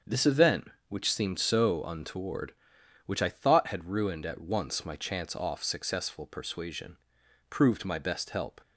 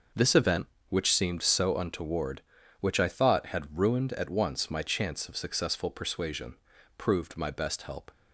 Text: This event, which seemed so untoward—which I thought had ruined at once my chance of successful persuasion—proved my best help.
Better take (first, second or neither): second